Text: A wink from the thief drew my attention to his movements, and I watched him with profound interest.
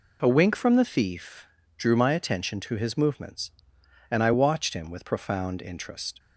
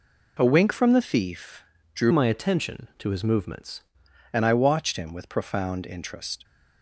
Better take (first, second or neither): first